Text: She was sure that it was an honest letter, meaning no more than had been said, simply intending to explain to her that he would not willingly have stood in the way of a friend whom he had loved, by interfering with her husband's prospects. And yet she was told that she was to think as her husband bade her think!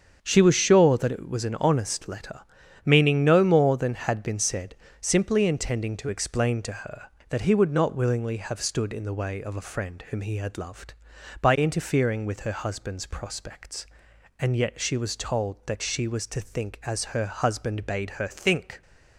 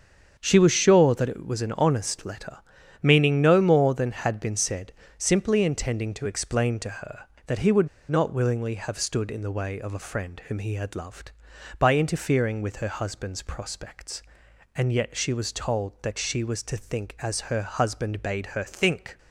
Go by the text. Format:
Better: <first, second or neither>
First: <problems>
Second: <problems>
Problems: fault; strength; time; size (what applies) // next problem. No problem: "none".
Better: first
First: starts louder than the rest; strong; until 1.2 s; 7 dB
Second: starts louder than the rest; strong; until 1.3 s; 7 dB // pauses between "would" and "not"; slight; at 7.8 s; 0.21 s long